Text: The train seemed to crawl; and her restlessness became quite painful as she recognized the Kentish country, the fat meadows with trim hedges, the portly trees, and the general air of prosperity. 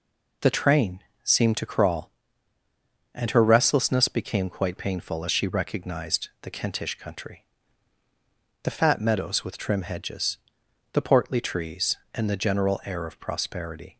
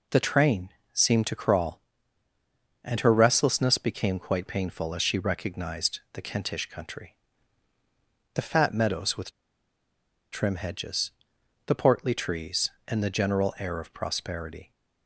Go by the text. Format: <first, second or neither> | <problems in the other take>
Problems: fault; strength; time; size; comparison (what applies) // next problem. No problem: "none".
first | pauses between "train" and "seemed"; slight; at 0.6 s; 0.24 s long; slight in the first // pauses between "with" and "trim"; at 9.2 s; 1.0 s long